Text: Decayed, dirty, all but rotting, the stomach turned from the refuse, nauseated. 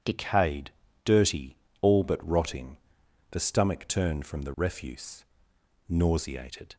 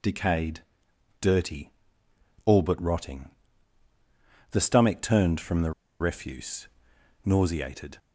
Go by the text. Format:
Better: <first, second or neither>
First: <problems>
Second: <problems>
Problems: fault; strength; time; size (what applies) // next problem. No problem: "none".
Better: first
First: none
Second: pauses between "the" and "refuse"; slight; at 5.7 s; 0.29 s long